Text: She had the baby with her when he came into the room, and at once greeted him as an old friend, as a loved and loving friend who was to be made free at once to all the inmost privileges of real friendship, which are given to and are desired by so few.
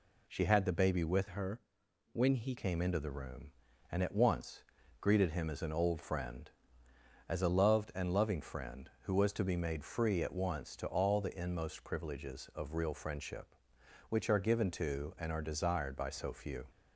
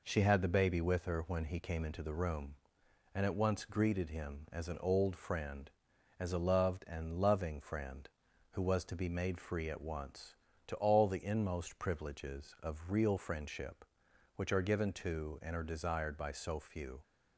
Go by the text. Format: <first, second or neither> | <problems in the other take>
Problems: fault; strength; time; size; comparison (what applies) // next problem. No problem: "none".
second | changes voice from "her" to "he"; from 1.2 to 2.5 s; 1.3 s long // pauses between "her" and "when"; noticeable; at 1.6 s; 0.52 s long // pauses between "once" and "greeted"; at 4.6 s; 0.38 s long